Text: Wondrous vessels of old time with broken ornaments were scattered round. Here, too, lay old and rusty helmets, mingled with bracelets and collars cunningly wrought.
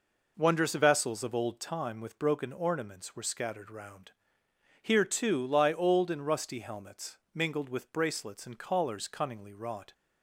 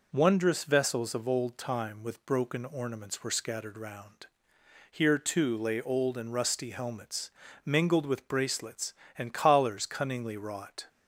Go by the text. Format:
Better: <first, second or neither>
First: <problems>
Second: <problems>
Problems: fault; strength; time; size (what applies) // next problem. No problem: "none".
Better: second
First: says "lie" for "lay"; at 5.4 s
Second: none